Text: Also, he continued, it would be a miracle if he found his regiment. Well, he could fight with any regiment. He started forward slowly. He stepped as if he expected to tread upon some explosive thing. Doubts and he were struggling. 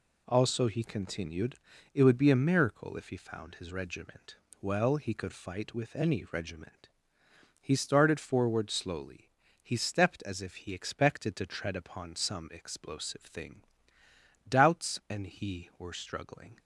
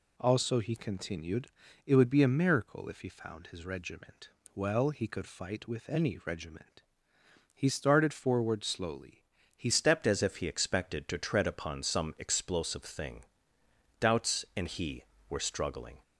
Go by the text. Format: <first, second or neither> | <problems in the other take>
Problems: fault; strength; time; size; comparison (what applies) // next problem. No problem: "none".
first | changes voice at "stepped"; from 9.7 s on; 6.3 s long